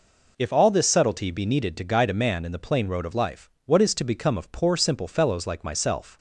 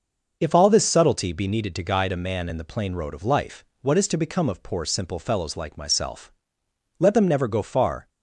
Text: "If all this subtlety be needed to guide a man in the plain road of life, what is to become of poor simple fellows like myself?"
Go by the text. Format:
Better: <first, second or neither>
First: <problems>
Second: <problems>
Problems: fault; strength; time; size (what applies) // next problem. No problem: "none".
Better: first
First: none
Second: starts louder than the rest; noticeable; until 1.4 s; 6 dB // goes on to say "Let them never go far"; noticeable; from 6.9 s on; 1.1 s long